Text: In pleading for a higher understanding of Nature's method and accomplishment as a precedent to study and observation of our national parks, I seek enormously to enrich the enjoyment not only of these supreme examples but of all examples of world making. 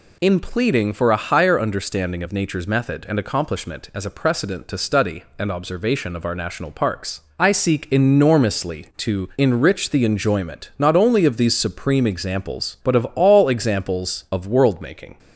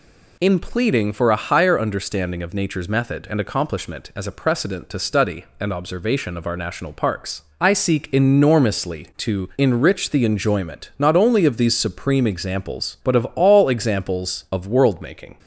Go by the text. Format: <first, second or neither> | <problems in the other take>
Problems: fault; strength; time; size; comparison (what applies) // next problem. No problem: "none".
neither | none